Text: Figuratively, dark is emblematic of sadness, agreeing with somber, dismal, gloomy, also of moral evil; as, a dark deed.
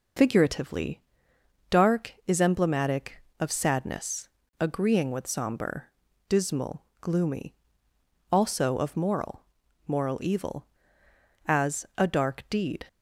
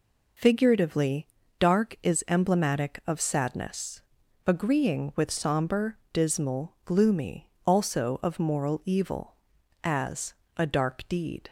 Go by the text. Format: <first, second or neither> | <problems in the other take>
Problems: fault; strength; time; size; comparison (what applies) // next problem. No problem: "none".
second | says "moral" twice; at 9.8 s